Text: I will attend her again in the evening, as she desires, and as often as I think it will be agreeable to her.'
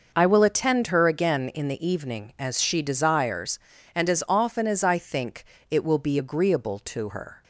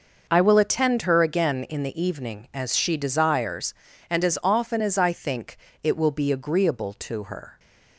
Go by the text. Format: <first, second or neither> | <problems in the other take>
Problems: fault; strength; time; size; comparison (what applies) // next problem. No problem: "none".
neither | pauses between "think" and "it"; slight; the same in both